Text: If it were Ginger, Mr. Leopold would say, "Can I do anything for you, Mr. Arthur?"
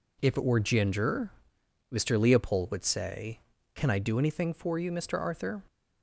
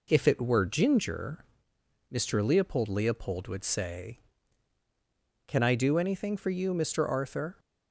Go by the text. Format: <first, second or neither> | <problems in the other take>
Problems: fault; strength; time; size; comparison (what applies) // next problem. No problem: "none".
first | says "Leopold" twice; at 2.8 s